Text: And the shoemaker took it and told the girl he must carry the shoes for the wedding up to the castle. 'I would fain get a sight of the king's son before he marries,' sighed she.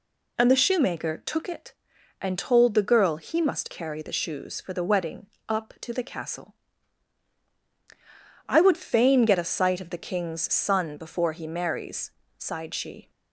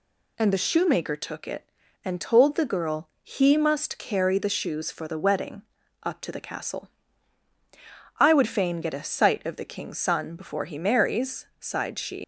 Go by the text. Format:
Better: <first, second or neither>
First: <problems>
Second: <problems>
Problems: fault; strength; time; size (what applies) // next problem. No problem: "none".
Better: first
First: pauses between "wedding" and "up"; slight; at 5.2 s; 0.20 s long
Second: pauses between "wedding" and "up"; at 5.6 s; 0.40 s long // leaves "she" unfinished; at 12.2 s; 110 ms